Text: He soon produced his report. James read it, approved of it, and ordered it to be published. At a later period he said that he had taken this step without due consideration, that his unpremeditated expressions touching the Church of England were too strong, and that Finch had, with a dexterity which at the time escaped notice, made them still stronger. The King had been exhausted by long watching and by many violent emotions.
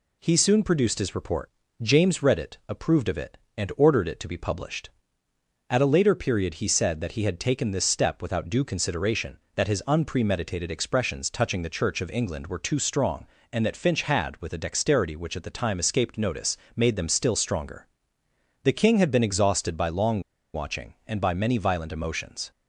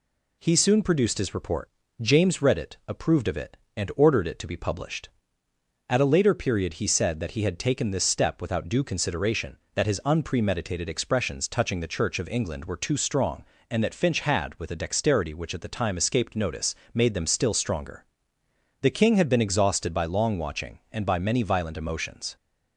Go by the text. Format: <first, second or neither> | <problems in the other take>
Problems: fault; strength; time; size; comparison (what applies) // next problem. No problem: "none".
second | pauses between "long" and "watching"; slight; at 20.2 s; 0.33 s long